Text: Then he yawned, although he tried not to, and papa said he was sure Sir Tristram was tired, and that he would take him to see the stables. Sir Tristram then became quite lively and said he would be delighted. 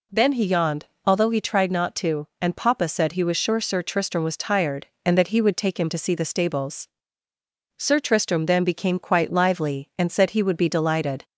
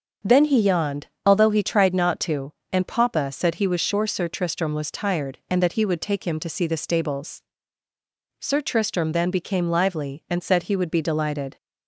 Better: first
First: none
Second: starts louder than the rest; until 1.4 s; 7 dB // skips "quite"; at 9.6 s

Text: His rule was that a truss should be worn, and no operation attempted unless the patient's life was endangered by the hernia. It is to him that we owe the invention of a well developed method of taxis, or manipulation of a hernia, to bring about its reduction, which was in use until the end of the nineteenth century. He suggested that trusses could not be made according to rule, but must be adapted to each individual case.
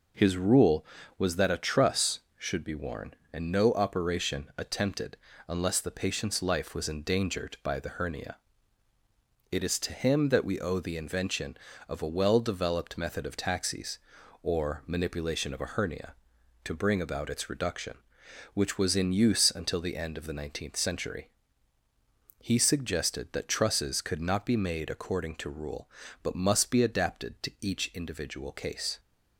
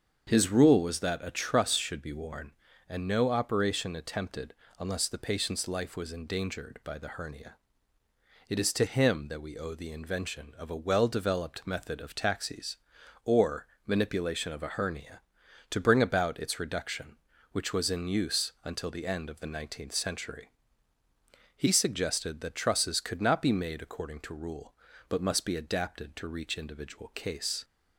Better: first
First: pauses between "attempted" and "unless"; slight; at 5.1 s; 0.28 s long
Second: starts louder than the rest; until 1.2 s; 7 dB // pauses between "attempted" and "unless"; slight; at 4.5 s; 0.26 s long // pauses between "or" and "manipulation"; slight; at 13.6 s; 0.18 s long // says "reach" for "each"; at 26.2 s

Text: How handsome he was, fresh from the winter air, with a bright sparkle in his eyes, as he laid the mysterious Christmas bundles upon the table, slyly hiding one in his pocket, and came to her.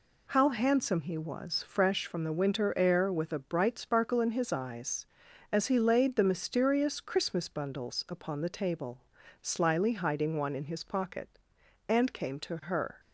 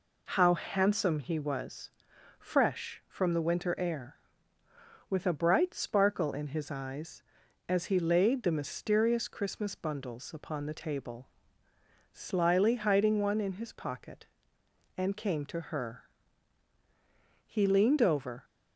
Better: first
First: none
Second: goes on to say "He leaned over"; noticeable; from 17.4 s on; 0.98 s long

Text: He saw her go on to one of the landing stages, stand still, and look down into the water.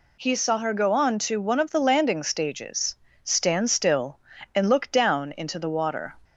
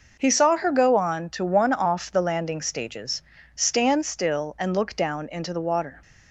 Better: first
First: none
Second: says "off" for "of"; at 1.7 s

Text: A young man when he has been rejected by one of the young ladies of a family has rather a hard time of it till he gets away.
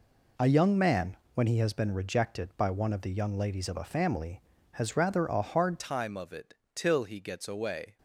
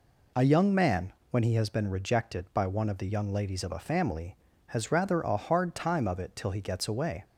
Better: second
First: pauses between "man" and "when"; slight; at 1.1 s; 0.20 s long // changes voice at "time"; from 5.7 s on; 2.2 s long // pauses between "it" and "till"; slight; at 6.5 s; 0.18 s long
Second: pauses between "man" and "when"; slight; at 1.1 s; 0.20 s long

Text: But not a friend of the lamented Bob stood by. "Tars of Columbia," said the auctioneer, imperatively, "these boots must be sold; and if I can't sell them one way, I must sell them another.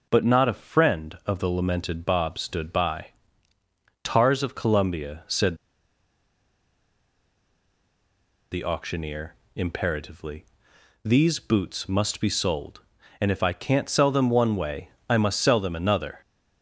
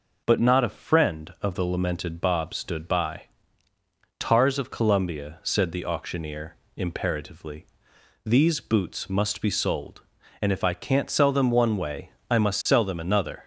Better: second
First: pauses between "said" and "the"; strong; at 5.5 s; 2.9 s long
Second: none

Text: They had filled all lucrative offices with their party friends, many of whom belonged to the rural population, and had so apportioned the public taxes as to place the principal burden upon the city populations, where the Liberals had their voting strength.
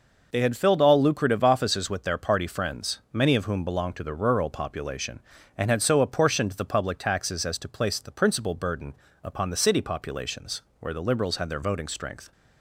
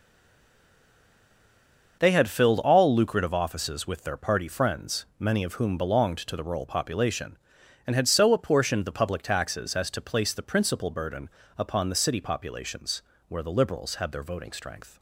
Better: first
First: pauses between "burden" and "upon"; slight; at 8.9 s; 0.28 s long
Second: stays silent before the first word; noticeable; until 2.0 s; 2.0 s long // starts louder than the rest; until 3.0 s; 6 dB // pauses between "burden" and "upon"; slight; at 11.2 s; 0.28 s long

